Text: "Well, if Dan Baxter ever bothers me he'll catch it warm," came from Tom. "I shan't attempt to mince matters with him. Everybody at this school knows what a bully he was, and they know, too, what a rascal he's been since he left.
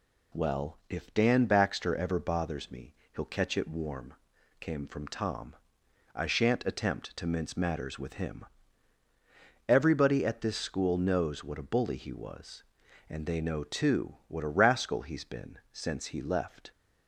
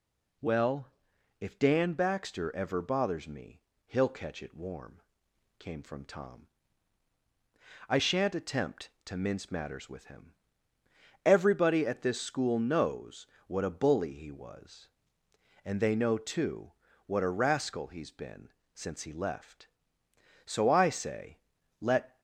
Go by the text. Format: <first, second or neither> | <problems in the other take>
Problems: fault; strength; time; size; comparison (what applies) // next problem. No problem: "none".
first | pauses between "me" and "he'll"; slight; at 3.6 s; 0.26 s long; slight in the first // pauses between "knows" and "what"; slight; at 13.2 s; 0.22 s long // pauses between "been" and "since"; slight; at 18.5 s; 0.24 s long // goes on to say "So I say let"; strong; from 20.4 s on; 1.7 s long